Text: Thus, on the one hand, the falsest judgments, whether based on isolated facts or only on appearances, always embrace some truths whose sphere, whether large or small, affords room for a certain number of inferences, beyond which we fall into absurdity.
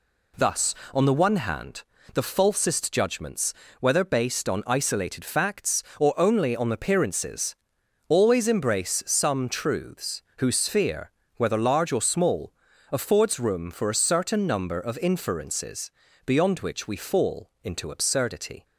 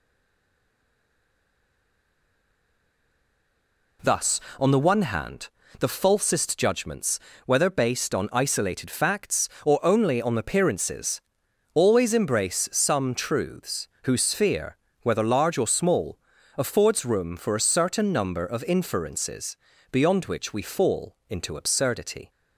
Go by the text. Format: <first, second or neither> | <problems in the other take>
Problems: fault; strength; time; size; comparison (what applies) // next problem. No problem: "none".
first | stays silent before the first word; strong; until 3.9 s; 3.9 s long // pauses between "truths" and "whose"; slight; at 13.8 s; 0.18 s long; slight in the first